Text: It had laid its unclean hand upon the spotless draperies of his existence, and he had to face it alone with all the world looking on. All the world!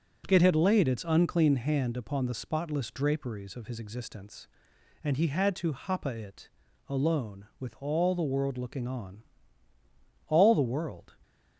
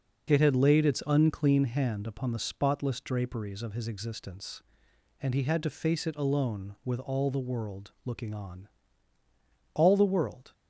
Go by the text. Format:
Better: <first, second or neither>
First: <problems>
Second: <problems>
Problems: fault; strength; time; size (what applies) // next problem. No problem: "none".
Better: second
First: says "hapa" for "face"; at 5.7 s // pauses between "it" and "alone"; at 6.4 s; 0.40 s long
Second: none